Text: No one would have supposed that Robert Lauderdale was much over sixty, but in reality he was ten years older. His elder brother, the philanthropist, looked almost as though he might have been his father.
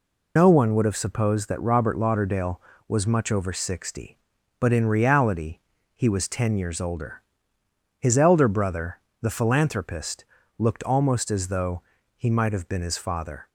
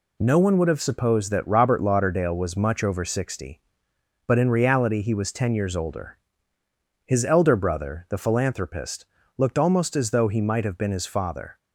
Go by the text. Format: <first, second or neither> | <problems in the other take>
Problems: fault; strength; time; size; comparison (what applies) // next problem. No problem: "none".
second | loses the start of "No"; at 0.3 s; 115 ms // pauses between "reality" and "he"; at 5.5 s; 0.38 s long // pauses between "though" and "he"; slight; at 11.8 s; 0.34 s long